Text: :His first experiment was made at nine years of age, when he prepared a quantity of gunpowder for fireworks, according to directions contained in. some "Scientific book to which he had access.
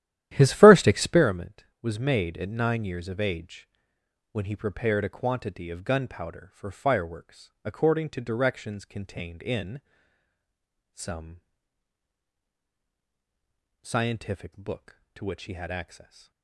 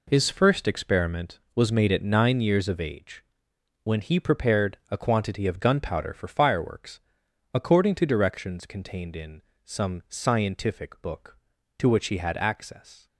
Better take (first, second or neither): second